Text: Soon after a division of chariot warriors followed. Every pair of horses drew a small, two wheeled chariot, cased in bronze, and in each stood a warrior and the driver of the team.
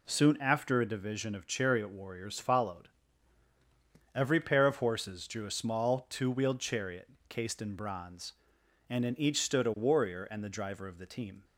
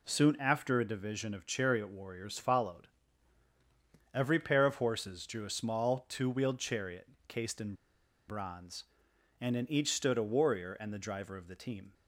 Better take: first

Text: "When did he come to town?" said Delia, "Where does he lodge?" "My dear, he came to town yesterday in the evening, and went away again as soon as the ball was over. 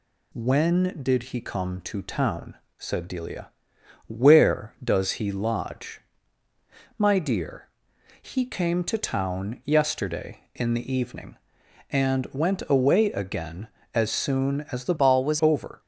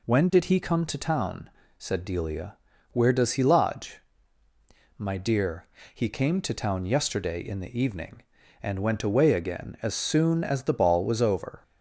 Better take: second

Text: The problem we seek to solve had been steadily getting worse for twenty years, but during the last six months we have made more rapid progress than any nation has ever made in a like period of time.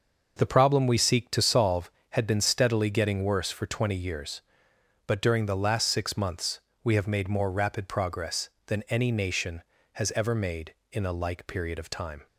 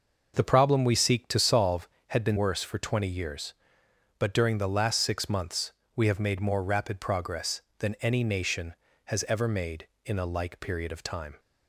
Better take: first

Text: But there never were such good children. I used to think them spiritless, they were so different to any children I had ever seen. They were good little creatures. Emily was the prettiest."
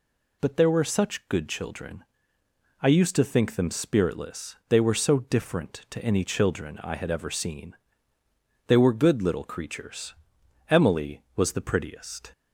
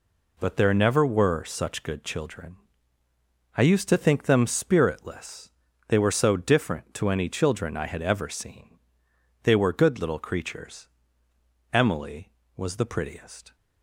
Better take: second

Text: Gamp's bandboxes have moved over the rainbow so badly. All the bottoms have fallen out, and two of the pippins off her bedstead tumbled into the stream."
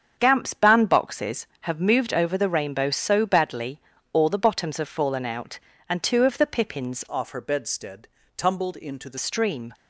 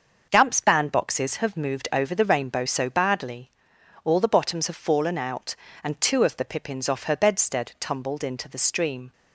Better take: second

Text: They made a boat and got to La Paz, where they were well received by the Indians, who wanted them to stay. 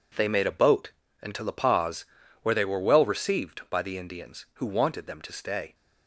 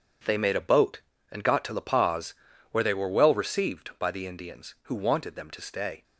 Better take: second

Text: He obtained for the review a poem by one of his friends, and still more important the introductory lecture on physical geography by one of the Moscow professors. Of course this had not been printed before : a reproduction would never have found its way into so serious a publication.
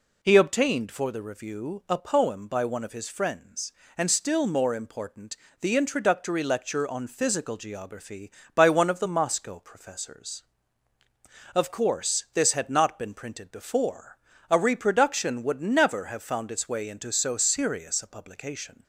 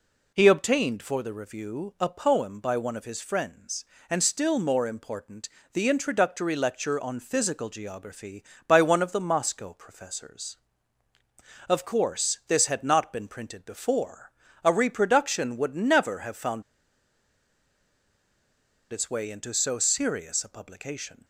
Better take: first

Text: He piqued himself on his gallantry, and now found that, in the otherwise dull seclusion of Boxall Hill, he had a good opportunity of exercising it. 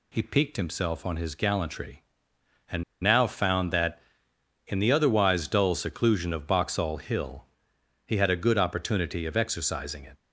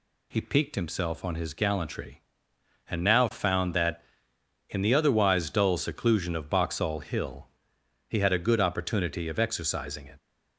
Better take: second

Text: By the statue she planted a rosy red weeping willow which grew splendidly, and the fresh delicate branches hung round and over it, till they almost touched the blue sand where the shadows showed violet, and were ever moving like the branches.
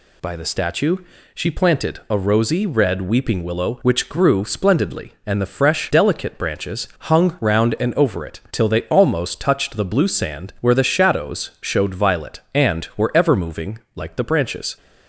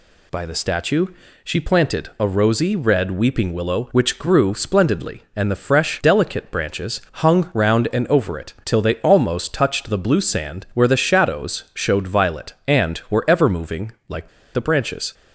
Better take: first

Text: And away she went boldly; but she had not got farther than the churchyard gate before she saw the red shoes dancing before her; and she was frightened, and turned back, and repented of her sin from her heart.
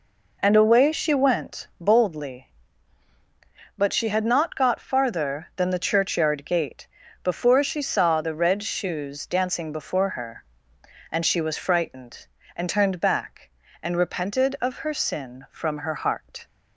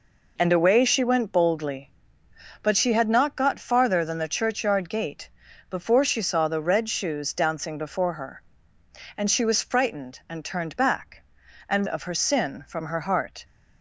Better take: first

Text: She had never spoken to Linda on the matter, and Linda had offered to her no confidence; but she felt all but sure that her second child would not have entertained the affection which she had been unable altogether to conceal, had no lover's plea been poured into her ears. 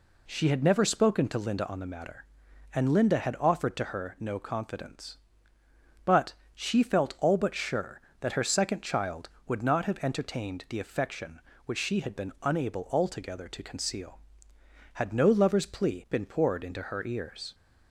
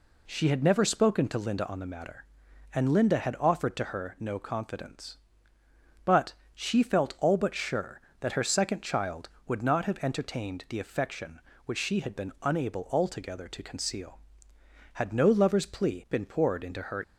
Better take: first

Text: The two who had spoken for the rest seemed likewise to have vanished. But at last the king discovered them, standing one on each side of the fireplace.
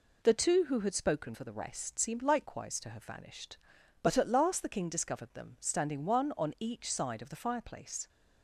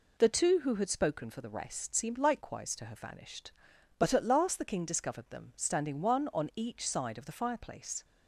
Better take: neither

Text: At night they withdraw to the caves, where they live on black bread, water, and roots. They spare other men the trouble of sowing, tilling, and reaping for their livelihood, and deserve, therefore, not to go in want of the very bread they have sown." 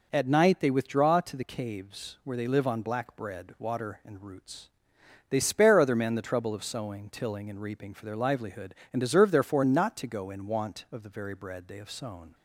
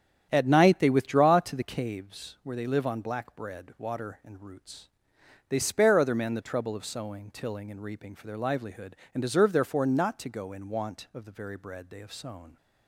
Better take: first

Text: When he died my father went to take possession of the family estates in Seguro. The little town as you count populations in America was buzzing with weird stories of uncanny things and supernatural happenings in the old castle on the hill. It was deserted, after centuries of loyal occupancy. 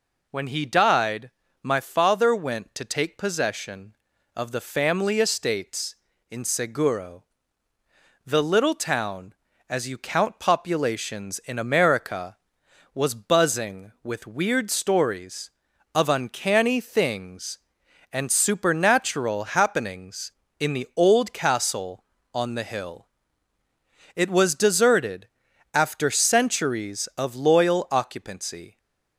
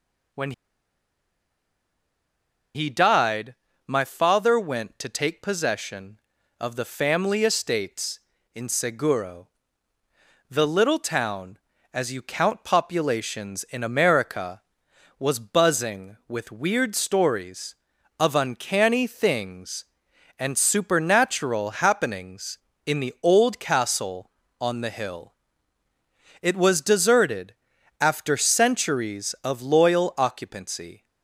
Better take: first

